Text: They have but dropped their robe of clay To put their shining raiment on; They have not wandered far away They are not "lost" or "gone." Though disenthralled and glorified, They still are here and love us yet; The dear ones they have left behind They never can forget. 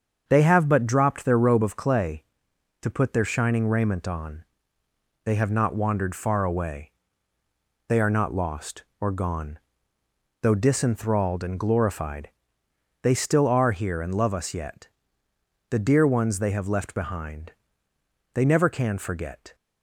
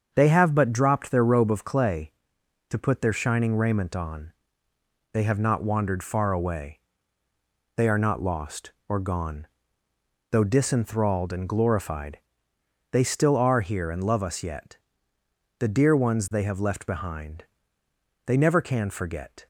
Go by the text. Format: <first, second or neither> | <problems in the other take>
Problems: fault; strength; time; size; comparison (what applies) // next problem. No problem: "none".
neither | starts louder than the rest; the same in both // pauses between "away" and "They"; noticeable; the same in both // pauses between "behind" and "They"; noticeable; the same in both